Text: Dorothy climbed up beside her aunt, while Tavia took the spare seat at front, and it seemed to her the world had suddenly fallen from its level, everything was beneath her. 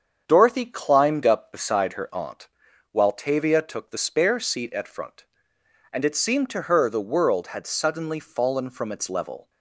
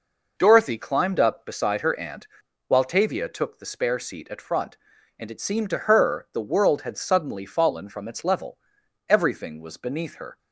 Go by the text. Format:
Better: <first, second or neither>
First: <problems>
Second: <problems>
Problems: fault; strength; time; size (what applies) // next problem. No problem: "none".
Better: second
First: starts louder than the rest; strong; until 1.2 s; 7.5 dB // stops before "everything was beneath her"; at 9.4 s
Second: none